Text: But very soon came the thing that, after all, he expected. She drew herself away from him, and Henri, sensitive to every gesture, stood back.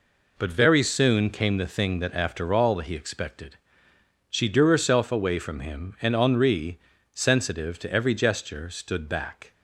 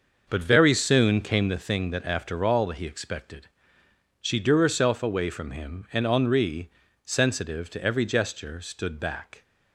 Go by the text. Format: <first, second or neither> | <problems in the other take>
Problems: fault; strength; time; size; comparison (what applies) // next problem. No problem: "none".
first | starts louder than the rest; until 1.7 s; 6 dB